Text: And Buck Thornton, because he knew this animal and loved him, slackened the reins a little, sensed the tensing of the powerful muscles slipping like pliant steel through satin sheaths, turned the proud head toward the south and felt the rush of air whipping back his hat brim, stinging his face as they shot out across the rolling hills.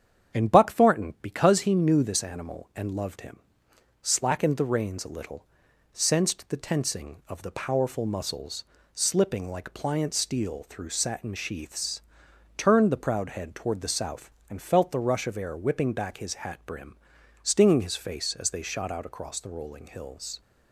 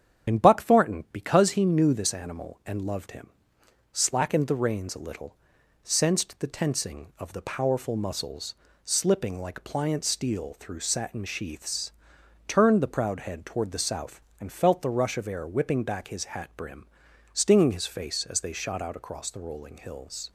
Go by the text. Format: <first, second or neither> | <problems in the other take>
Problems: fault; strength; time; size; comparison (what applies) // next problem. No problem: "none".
first | loses the start of "And"; at 0.2 s; 25 ms // starts louder than the rest; strong; until 1.3 s; 9 dB; strong in the first // pauses between "muscles" and "slipping"; slight; at 8.5 s; 0.30 s long; slight in the first